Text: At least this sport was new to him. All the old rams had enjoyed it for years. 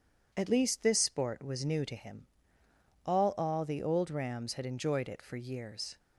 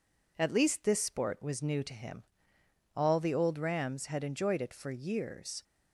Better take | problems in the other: second | says "All" twice; at 3.3 s

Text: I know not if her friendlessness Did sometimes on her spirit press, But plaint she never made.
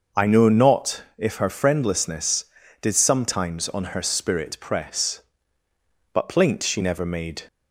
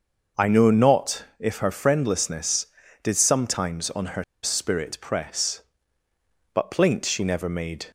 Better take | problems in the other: first | starts louder than the rest; noticeable; until 1.5 s; 6 dB; noticeable in the first // pauses between "her" and "spirit"; slight; at 4.2 s; 0.19 s long

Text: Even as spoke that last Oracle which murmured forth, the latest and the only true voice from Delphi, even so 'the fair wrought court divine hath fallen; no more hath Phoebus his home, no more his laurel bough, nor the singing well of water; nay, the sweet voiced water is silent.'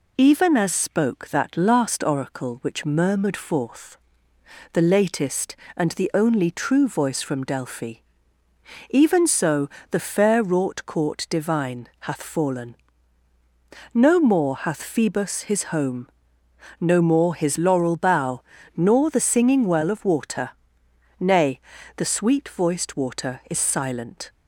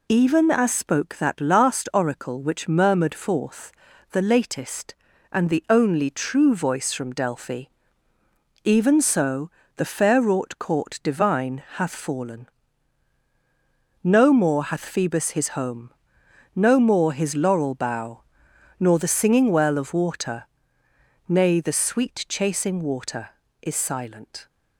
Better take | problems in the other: first | pauses between "so" and "the"; slight; at 9.4 s; 0.28 s long; slight in the first // says "chasing" for "voiced"; at 22.2 s

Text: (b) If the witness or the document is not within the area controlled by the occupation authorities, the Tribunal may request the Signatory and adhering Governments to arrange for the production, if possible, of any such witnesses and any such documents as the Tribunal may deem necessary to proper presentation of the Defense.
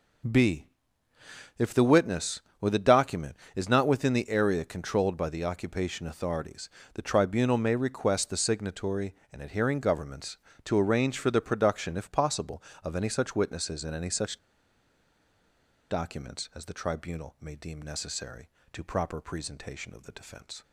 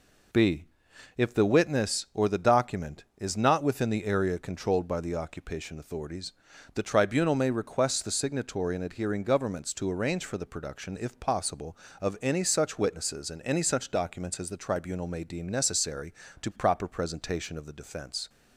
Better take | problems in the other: second | pauses between "such" and "documents"; strong; at 14.3 s; 1.5 s long

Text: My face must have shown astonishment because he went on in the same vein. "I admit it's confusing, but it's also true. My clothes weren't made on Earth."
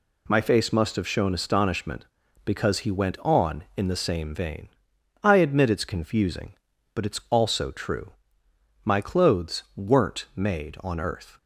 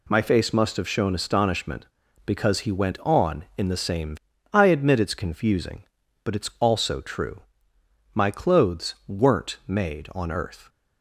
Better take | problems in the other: first | skips "vein"; at 4.3 s

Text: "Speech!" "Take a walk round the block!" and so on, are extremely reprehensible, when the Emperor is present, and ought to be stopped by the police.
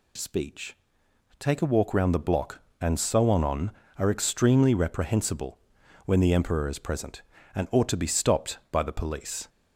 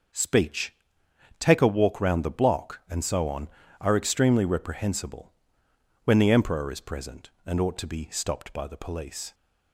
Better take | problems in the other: second | says "on" twice; at 3.4 s

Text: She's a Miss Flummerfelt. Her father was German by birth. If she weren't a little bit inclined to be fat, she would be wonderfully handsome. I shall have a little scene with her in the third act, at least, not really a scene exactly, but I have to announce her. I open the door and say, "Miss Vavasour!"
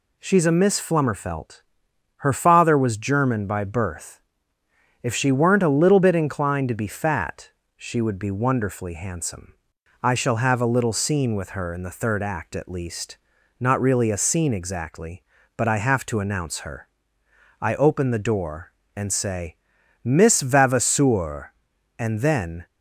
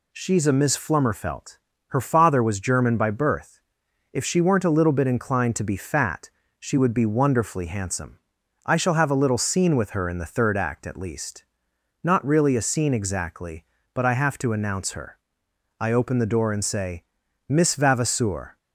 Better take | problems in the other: second | goes on to say "and then"; noticeable; from 21.9 s on; 0.66 s long

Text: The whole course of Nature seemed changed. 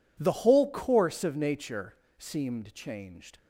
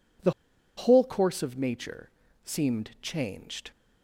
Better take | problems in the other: first | pauses between "The" and "whole"; noticeable; at 0.3 s; 0.46 s long // pauses between "Nature" and "seemed"; slight; at 2.0 s; 0.34 s long; slight in the first

